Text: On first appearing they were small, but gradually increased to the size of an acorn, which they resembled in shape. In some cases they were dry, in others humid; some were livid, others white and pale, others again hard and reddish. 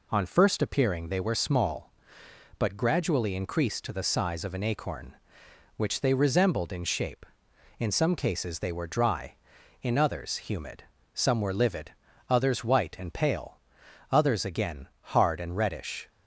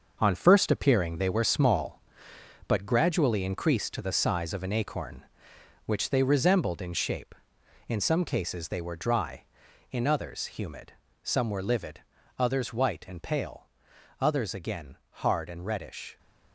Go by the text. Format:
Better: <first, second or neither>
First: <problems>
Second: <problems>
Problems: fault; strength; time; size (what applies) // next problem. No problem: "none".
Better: first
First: none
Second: gets quieter; strong; throughout; 8.5 dB